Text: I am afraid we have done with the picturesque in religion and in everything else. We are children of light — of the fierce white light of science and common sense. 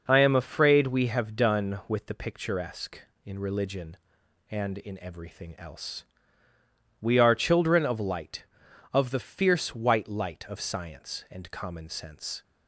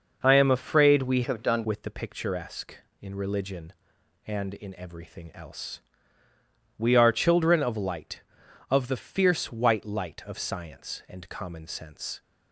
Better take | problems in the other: first | changes voice from "have" to "done"; from 1.2 to 1.6 s; 0.4 s long

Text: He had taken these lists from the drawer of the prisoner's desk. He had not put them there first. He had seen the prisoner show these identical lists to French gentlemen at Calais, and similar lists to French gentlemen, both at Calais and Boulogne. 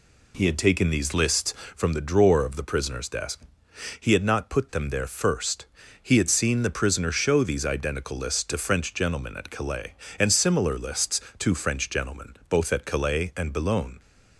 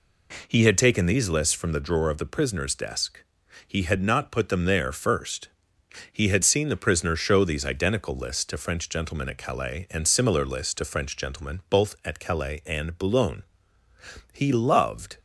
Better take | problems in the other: first | goes on to say "He loved"; noticeable; from 14.3 s on; 0.86 s long

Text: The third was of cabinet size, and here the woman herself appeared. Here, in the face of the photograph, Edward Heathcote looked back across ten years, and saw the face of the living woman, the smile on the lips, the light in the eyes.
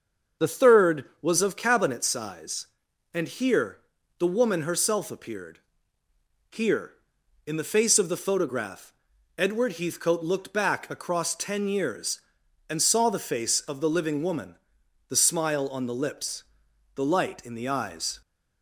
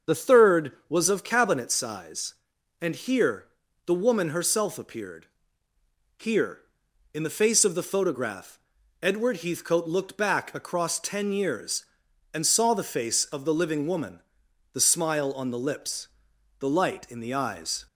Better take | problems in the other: neither | starts louder than the rest; the same in both // pauses between "here" and "the"; the same in both

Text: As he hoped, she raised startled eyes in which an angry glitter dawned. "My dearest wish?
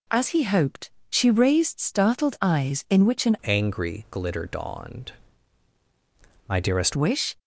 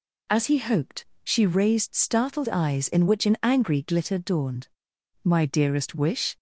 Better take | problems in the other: second | changes voice from "angry" to "dearest"; from 3.4 to 6.9 s; 3.5 s long

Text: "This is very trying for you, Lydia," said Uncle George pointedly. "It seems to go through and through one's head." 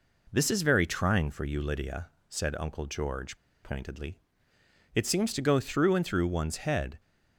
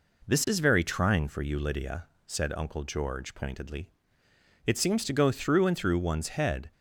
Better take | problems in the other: second | pauses between "George" and "pointedly"; slight; at 3.3 s; 0.27 s long

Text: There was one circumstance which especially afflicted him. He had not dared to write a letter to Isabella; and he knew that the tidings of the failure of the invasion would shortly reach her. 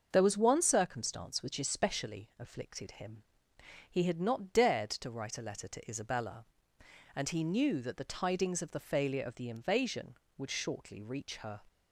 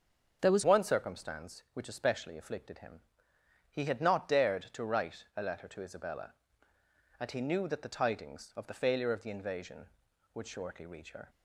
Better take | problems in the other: first | starts louder than the rest; until 1.4 s; 6.5 dB; also in the first // changes voice at "one"; from 0.6 s on; 10.6 s long

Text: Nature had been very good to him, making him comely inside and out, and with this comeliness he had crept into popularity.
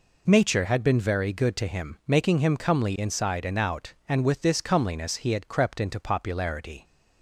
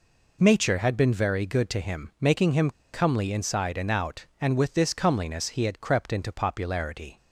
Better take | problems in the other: first | pauses between "him" and "comely"; slight; at 2.6 s; 0.23 s long

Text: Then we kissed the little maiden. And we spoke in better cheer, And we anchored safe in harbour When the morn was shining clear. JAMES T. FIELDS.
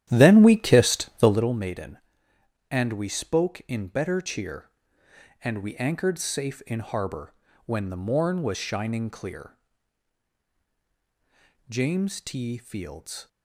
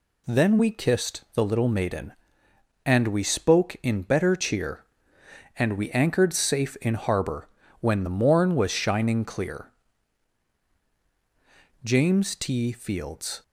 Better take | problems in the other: second | starts louder than the rest; strong; until 1.5 s; 12 dB // pauses between "harbour" and "When"; slight; at 7.3 s; 0.32 s long; slight in the second

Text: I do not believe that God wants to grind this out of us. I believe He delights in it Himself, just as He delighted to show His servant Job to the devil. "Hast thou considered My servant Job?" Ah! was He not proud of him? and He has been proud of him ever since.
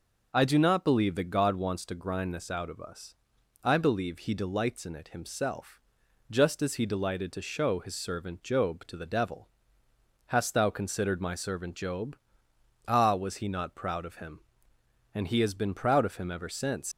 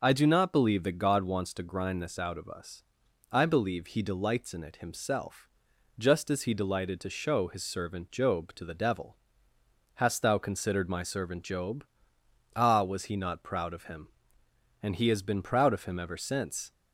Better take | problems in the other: second | leaves "since" unfinished; at 16.9 s; 125 ms

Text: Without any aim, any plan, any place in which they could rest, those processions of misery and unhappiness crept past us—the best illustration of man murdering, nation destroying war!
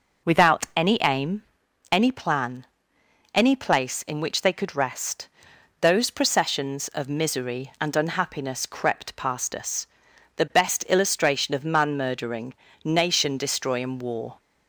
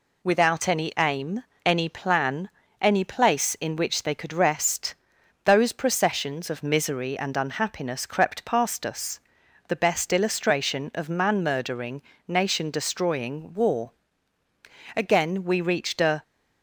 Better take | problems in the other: first | goes on to say "Again we reached a"; noticeable; from 14.9 s on; 1.2 s long

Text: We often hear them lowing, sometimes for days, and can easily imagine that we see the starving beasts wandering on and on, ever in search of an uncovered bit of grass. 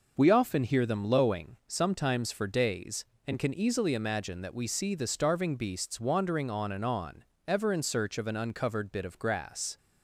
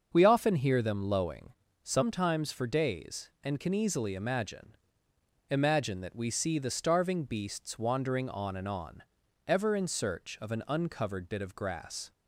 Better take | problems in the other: first | starts louder than the rest; until 1.1 s; 6.5 dB // says "imagine" twice; at 5.4 s

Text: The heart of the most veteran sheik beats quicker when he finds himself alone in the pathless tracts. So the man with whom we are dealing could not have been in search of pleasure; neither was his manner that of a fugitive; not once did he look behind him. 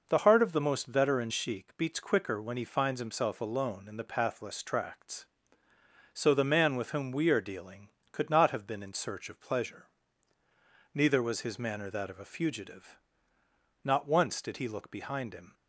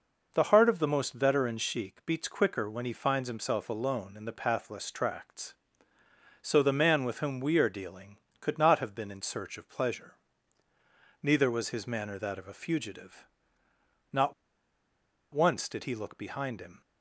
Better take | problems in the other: first | pauses between "not" and "once"; at 14.3 s; 1.0 s long

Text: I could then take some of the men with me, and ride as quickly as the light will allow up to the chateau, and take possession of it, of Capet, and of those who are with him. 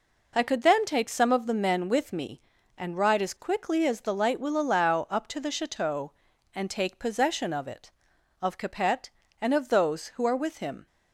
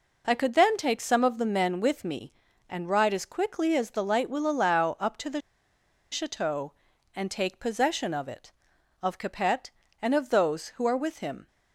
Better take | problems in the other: first | pauses between "the" and "chateau"; noticeable; at 5.3 s; 0.72 s long

